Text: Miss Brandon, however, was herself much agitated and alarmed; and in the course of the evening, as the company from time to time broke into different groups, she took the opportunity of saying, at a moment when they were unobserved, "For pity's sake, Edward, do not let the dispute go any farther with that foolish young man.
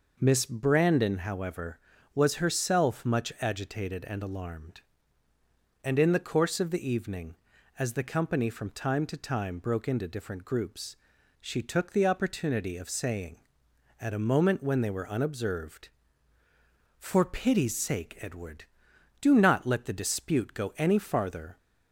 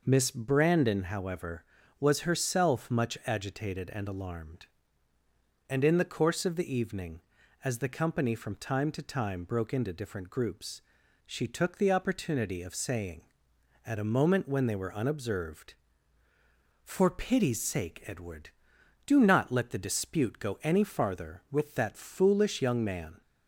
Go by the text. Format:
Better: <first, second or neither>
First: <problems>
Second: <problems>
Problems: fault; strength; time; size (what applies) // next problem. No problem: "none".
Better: second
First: stops before "with that foolish young man"; at 21.5 s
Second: none